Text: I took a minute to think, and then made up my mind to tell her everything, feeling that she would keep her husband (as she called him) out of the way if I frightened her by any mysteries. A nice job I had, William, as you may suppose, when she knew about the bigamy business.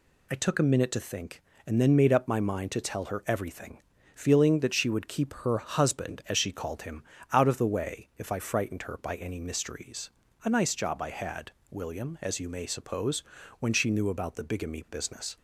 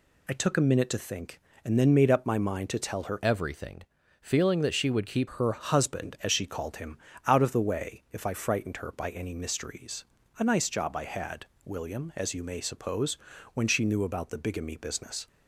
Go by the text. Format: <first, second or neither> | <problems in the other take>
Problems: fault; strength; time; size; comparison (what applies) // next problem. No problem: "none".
first | changes voice from "everything" to "keep"; from 3.2 to 5.2 s; 2.0 s long